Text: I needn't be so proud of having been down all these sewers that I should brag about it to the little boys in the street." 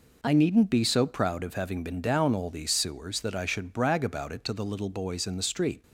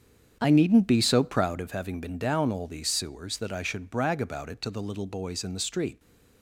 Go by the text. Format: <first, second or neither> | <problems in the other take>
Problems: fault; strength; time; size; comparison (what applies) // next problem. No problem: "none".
first | starts louder than the rest; strong; until 1.7 s; 8 dB